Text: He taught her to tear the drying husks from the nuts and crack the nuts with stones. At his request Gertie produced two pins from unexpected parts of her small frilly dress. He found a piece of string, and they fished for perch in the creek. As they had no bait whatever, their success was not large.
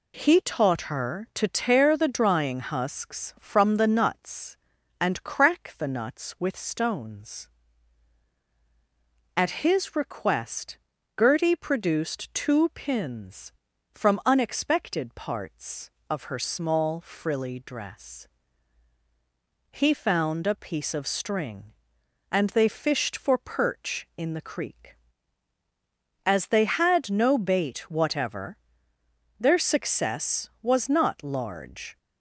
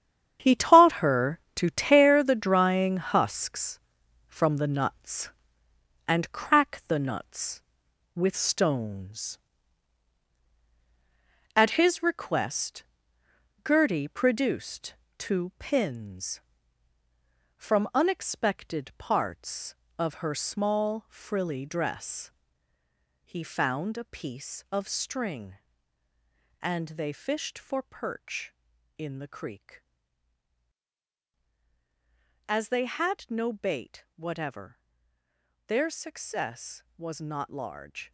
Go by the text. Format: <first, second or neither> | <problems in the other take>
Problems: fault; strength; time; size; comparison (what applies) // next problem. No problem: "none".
first | gets quieter; strong; throughout; 10.5 dB // pauses between "request" and "Gertie"; noticeable; at 12.8 s; 0.82 s long; also in the first // pauses between "produced" and "two"; slight; at 14.9 s; 0.24 s long